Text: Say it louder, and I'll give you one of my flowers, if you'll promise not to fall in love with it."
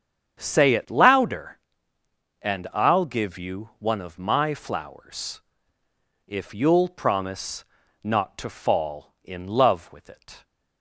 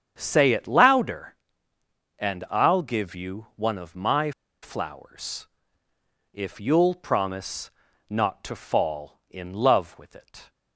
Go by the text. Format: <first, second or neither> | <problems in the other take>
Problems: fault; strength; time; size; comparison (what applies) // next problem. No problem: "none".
first | starts louder than the rest; strong; until 1.1 s; 8 dB; strong in the first // pauses between "my" and "flowers"; slight; at 4.3 s; 0.31 s long // pauses between "promise" and "not"; slight; at 7.7 s; 0.36 s long; slight in the first